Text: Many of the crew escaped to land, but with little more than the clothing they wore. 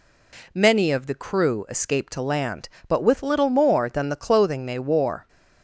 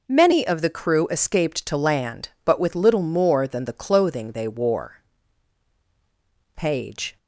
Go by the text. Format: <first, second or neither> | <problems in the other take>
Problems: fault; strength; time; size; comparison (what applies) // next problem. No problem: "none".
first | goes on to say "Page"; noticeable; from 6.5 s on; 0.62 s long